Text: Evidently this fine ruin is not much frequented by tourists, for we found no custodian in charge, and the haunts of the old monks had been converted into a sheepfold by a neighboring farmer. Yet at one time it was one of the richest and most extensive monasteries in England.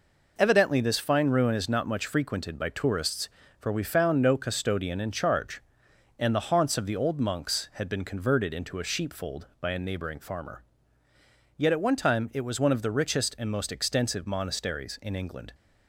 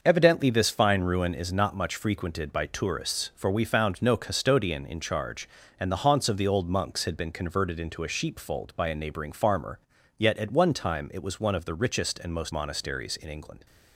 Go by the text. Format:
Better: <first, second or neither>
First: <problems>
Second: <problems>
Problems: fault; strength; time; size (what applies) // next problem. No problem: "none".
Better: first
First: none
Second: starts louder than the rest; noticeable; until 1.0 s; 6 dB // skips "extensive"; at 12.5 s